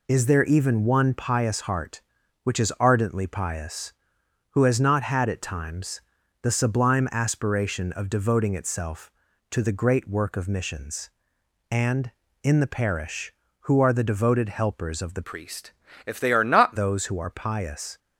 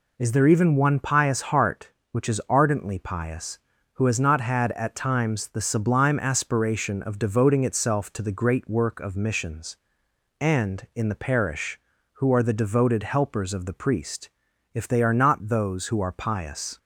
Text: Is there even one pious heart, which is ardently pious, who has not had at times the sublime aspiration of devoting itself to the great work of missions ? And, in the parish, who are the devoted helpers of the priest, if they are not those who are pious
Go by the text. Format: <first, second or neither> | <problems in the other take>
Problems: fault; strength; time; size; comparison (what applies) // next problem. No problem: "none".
second | pauses between "times" and "the"; at 6.0 s; 0.42 s long // changes voice from "priest" to "not"; from 15.2 to 16.7 s; 1.5 s long